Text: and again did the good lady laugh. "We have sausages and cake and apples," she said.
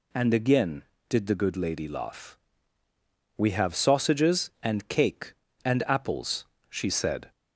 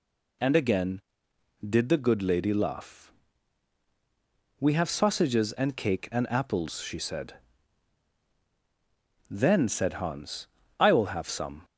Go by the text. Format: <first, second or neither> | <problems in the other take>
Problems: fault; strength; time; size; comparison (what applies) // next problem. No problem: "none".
first | goes on to say "Then said Hans I will have some"; strong; from 9.2 s on; 2.3 s long